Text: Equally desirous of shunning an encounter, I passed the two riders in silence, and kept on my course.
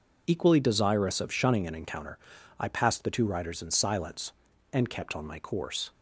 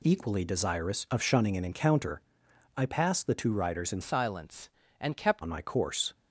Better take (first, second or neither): first